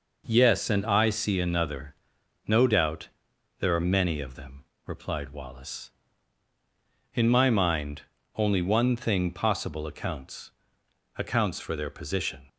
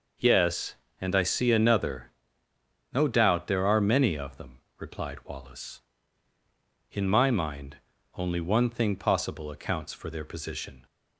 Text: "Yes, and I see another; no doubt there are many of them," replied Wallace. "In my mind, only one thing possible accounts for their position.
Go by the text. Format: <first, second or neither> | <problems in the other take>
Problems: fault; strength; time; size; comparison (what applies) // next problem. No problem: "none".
second | pauses between "doubt" and "there"; noticeable; at 3.0 s; 0.50 s long // says "accounts" twice; at 11.1 s